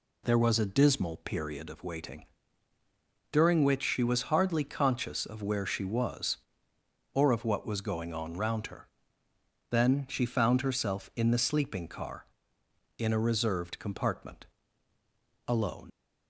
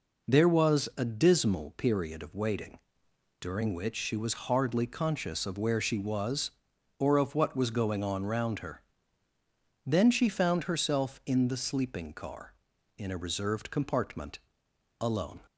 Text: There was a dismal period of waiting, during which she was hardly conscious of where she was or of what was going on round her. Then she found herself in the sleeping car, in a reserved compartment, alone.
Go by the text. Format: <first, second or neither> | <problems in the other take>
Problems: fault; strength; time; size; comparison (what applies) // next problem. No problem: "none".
second | leaves "alone" unfinished; at 15.9 s; 105 ms